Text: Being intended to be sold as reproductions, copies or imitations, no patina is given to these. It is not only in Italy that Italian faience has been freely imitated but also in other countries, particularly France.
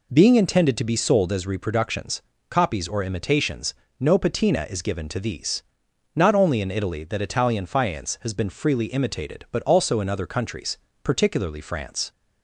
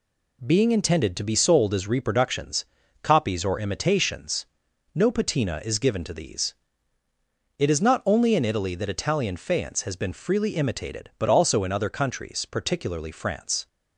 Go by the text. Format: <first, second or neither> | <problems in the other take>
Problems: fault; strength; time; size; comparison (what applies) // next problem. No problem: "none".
second | skips "It is"; at 5.8 s